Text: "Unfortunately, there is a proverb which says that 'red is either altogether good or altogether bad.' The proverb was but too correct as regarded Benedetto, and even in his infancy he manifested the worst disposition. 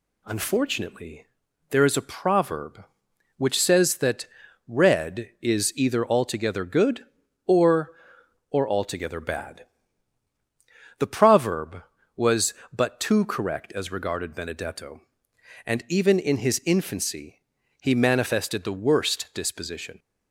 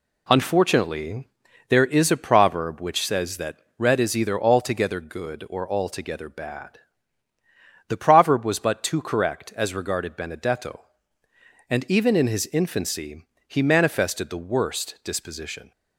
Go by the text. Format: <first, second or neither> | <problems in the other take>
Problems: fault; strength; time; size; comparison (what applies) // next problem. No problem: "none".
second | pauses between "that" and "red"; at 4.2 s; 0.40 s long; slight in the second // says "or" twice; at 8.4 s // pauses between "infancy" and "he"; at 17.4 s; 0.40 s long; slight in the second